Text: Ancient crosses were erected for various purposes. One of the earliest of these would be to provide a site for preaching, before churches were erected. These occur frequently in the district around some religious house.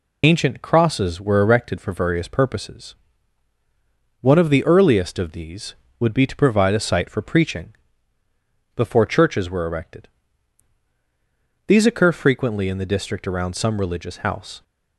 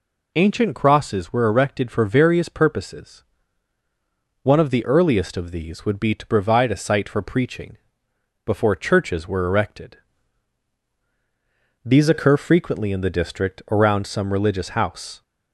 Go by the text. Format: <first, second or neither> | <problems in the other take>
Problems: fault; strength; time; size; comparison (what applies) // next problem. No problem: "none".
second | loses the start of "Ancient"; at 0.2 s; 50 ms